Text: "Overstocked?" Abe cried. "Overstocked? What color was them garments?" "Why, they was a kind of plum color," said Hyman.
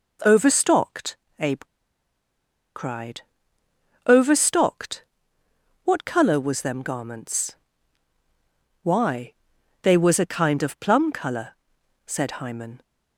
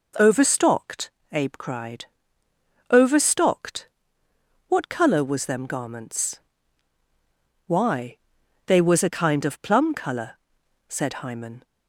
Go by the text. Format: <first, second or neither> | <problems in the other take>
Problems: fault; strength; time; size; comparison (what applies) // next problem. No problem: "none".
second | pauses between "Abe" and "cried"; at 1.6 s; 1.1 s long